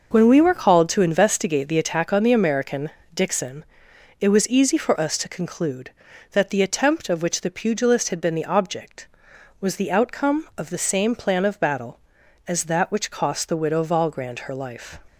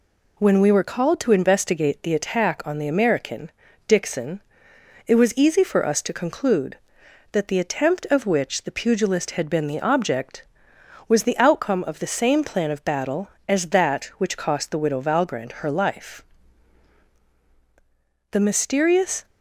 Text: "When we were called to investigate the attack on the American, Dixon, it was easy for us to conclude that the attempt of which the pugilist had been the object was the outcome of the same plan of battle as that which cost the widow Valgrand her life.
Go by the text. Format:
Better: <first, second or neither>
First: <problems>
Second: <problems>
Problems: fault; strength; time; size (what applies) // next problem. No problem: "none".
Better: first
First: none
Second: goes on to say "The mysterious"; noticeable; from 18.3 s on; 0.94 s long